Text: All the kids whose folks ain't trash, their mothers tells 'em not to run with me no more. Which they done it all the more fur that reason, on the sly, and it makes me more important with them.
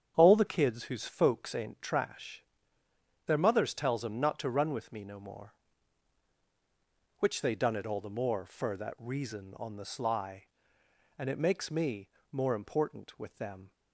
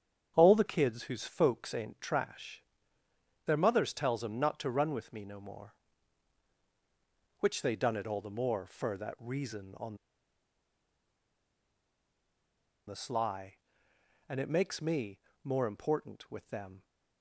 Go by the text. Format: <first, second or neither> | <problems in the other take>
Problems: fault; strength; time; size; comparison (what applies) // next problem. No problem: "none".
first | starts louder than the rest; strong; until 1.3 s; 8.5 dB; strong in the first // pauses between "on" and "the"; strong; at 9.9 s; 2.9 s long // pauses between "me" and "more"; slight; at 15.1 s; 0.22 s long; slight in the first